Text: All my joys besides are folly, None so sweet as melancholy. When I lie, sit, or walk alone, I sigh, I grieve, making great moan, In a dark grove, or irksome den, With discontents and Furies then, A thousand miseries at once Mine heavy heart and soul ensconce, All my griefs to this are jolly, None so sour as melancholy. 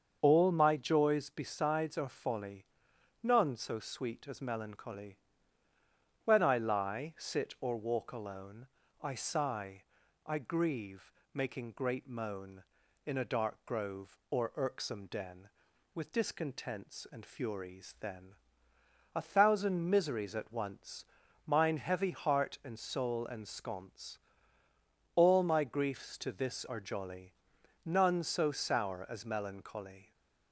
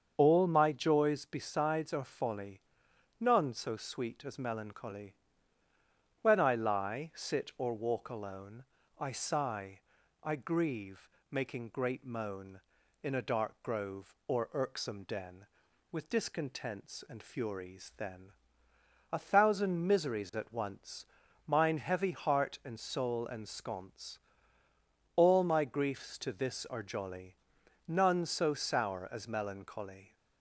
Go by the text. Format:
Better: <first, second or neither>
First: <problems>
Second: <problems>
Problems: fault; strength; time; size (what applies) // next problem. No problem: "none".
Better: neither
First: starts louder than the rest; until 1.2 s; 7 dB // pauses between "once" and "Mine"; at 21.0 s; 0.42 s long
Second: starts louder than the rest; until 1.1 s; 7 dB // pauses between "once" and "Mine"; at 21.0 s; 0.42 s long